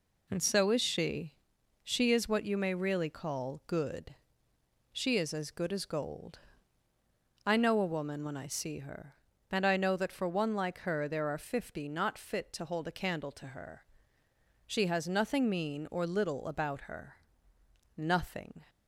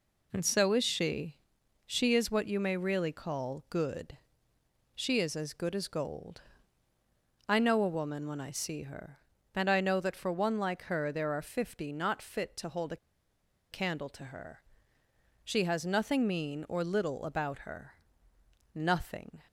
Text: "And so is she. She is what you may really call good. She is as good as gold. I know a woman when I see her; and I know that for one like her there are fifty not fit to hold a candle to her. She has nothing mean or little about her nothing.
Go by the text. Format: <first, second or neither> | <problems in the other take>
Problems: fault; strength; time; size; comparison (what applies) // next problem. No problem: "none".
first | pauses between "a" and "candle"; noticeable; at 12.9 s; 0.75 s long // pauses between "her" and "nothing"; noticeable; at 17.9 s; 0.78 s long; noticeable in the first